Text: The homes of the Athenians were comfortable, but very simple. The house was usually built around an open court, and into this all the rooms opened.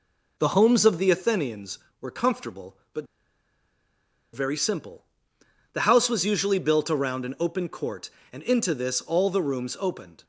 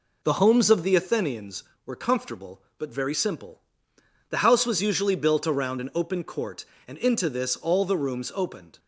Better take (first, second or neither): second